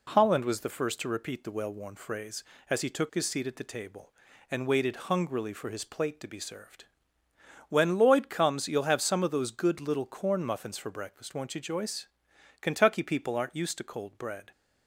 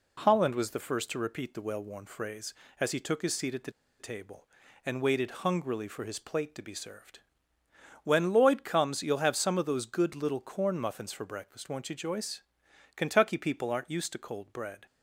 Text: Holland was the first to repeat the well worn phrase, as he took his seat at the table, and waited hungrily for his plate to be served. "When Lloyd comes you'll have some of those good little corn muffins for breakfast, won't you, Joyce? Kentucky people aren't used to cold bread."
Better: first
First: none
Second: pauses between "the" and "table"; slight; at 3.7 s; 0.29 s long

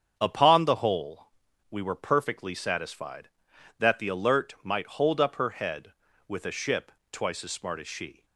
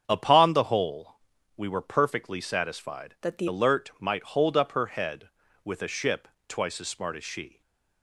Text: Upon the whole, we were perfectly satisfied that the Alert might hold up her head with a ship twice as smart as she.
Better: first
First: starts louder than the rest; strong; until 1.1 s; 7.5 dB // pauses between "ship" and "twice"; slight; at 6.9 s; 0.22 s long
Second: starts louder than the rest; strong; until 1.0 s; 7.5 dB // changes voice from "that" to "the"; from 3.2 to 3.4 s; 0.2 s long // pauses between "ship" and "twice"; slight; at 6.2 s; 0.22 s long // stays silent after the last word; slight; from 7.4 s on; 0.6 s long

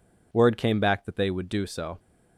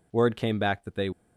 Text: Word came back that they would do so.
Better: first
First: none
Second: stops before "would do so"; at 1.1 s

